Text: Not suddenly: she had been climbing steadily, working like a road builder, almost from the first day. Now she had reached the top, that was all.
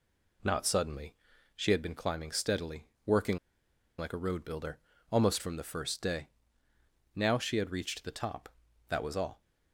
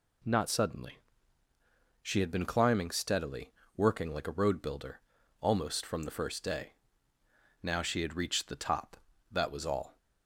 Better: second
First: pauses between "working" and "like"; noticeable; at 3.3 s; 0.61 s long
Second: none

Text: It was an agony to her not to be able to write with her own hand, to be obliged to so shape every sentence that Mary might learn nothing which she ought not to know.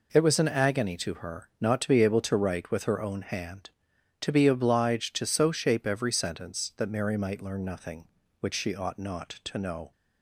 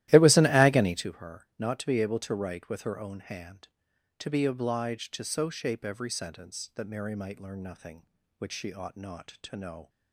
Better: first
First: none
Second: starts louder than the rest; strong; until 1.1 s; 15 dB

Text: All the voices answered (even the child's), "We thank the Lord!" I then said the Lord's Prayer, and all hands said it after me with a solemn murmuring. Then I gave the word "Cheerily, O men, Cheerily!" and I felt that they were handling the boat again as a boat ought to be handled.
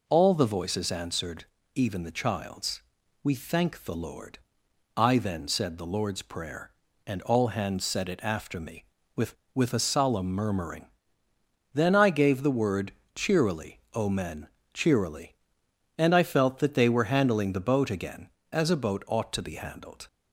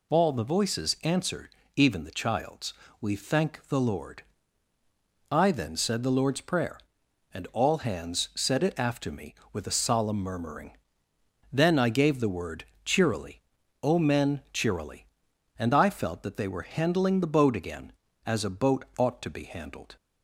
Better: second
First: says "with" twice; at 9.5 s // pauses between "word" and "Cheerily"; slight; at 12.9 s; 0.24 s long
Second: pauses between "word" and "Cheerily"; slight; at 12.6 s; 0.20 s long

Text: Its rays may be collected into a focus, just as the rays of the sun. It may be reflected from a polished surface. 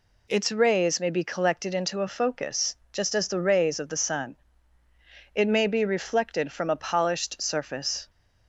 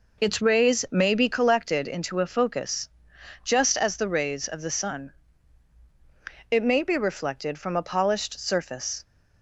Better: neither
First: none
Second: none

